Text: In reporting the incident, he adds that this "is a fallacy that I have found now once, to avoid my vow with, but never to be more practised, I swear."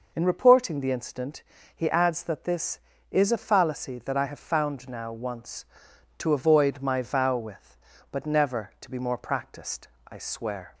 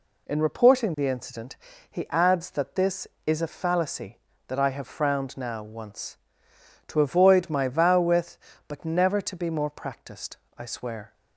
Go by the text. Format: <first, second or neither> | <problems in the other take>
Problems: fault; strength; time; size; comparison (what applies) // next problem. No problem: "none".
first | says "frowned" for "found"; at 4.8 s